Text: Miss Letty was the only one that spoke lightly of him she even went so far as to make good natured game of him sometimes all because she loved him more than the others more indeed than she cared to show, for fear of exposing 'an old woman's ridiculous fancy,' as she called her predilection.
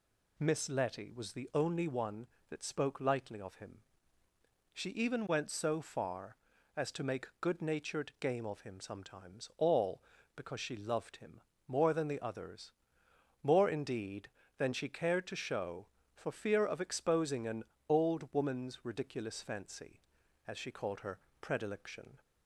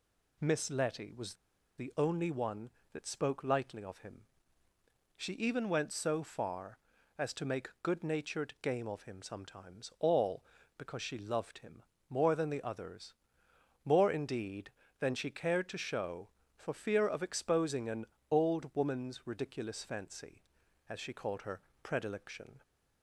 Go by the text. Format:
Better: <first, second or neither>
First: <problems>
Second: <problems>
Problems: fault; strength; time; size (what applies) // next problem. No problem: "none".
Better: first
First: pauses between "him" and "she"; noticeable; at 3.7 s; 0.94 s long // pauses between "him" and "more"; slight; at 11.3 s; 0.26 s long // pauses between "others" and "more"; noticeable; at 12.6 s; 0.72 s long // pauses between "an" and "old"; slight; at 17.6 s; 0.26 s long // pauses between "her" and "predilection"; slight; at 21.1 s; 0.20 s long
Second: pauses between "was" and "the"; at 1.3 s; 0.44 s long // pauses between "him" and "she"; noticeable; at 4.2 s; 0.94 s long // pauses between "him" and "more"; slight; at 11.8 s; 0.26 s long // pauses between "others" and "more"; noticeable; at 13.1 s; 0.72 s long // pauses between "an" and "old"; slight; at 18.0 s; 0.26 s long // pauses between "her" and "predilection"; slight; at 21.6 s; 0.20 s long